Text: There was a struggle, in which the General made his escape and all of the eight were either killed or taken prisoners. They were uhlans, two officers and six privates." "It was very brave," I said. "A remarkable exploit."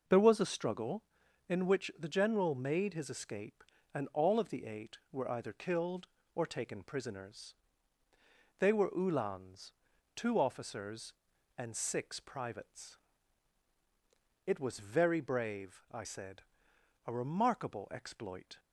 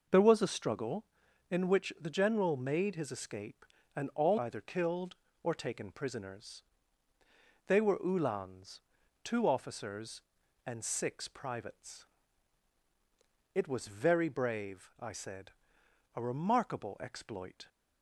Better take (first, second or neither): first